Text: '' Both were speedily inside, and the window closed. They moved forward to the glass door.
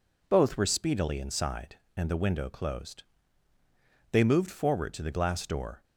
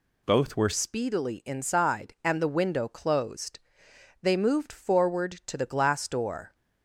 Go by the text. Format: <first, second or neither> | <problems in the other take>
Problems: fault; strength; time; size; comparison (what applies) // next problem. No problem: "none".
first | changes voice at "speedily"; from 0.7 s on; 5.8 s long